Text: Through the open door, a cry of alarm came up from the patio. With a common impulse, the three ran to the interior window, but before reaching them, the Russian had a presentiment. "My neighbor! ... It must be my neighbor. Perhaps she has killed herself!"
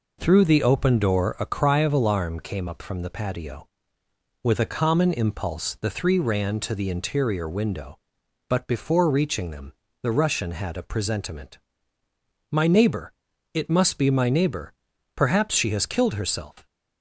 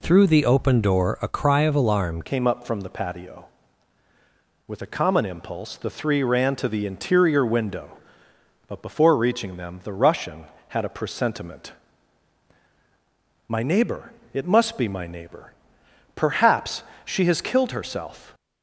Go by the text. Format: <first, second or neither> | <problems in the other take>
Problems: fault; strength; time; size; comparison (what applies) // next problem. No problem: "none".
first | changes voice at "came"; from 2.2 s on; 16.1 s long // pauses between "Perhaps" and "she"; slight; at 16.8 s; 0.24 s long